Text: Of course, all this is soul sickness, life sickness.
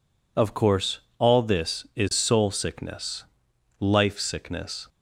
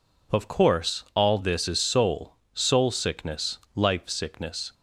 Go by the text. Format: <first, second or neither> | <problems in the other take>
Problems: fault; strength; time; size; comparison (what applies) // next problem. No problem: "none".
first | says "soul" twice; at 2.5 s